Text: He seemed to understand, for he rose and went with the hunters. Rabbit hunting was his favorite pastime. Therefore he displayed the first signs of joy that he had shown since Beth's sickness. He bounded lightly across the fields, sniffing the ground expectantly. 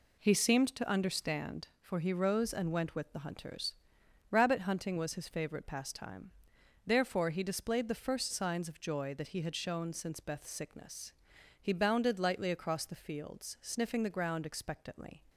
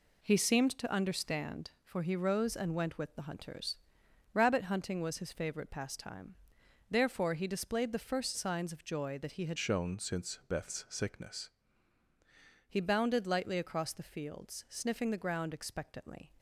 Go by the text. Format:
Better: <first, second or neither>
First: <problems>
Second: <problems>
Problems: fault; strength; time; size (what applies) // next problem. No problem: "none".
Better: first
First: none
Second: changes voice from "shown" to "sickness"; from 9.5 to 11.4 s; 1.9 s long